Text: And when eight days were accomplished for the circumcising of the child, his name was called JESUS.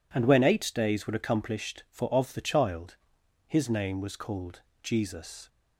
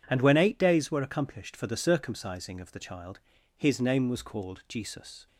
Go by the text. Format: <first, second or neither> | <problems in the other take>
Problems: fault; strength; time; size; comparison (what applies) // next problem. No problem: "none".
second | skips "the circumcising"; at 2.1 s // pauses between "called" and "JESUS"; slight; at 4.5 s; 0.24 s long